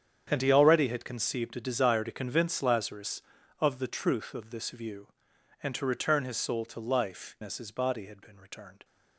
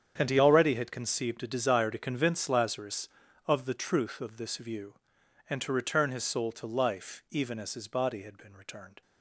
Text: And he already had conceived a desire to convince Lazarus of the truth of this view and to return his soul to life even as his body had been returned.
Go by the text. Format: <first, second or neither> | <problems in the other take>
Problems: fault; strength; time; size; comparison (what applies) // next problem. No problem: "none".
second | starts louder than the rest; strong; until 1.3 s; 8.5 dB; strong in the second // skips "even"; at 7.3 s